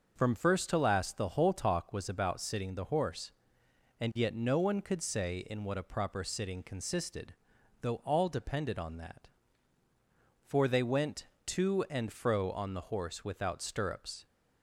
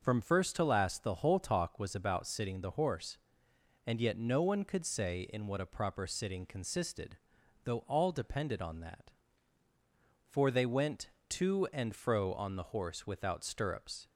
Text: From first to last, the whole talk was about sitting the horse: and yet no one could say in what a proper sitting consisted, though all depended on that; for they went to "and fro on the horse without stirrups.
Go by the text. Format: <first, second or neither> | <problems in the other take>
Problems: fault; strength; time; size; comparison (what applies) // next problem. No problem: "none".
neither | starts louder than the rest; the same in both